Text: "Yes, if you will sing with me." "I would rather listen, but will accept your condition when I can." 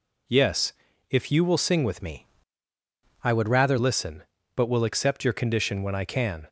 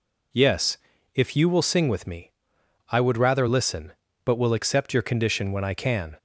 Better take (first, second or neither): second